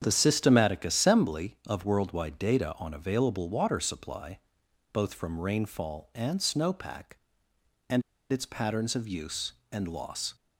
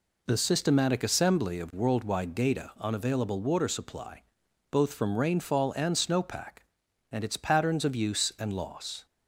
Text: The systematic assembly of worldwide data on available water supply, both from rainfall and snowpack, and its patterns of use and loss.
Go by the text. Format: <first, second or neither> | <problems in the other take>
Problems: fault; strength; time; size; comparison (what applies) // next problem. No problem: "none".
second | starts louder than the rest; strong; until 1.0 s; 8 dB // pauses between "and" and "its"; slight; at 8.0 s; 0.29 s long